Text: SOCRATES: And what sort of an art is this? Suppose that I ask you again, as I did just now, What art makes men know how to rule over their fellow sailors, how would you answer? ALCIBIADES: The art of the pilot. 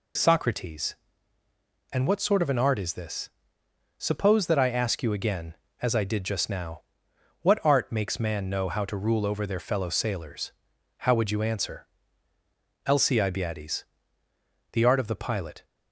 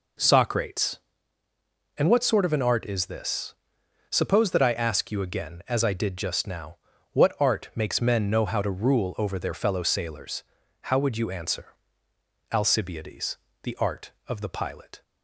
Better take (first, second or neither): second